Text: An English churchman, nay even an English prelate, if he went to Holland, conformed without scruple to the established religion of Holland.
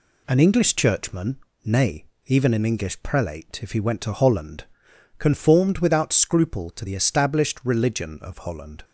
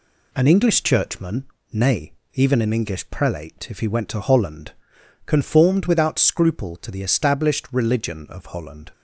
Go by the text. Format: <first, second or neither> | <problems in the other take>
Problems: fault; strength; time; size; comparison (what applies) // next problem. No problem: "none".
neither | pauses between "nay" and "even"; slight; the same in both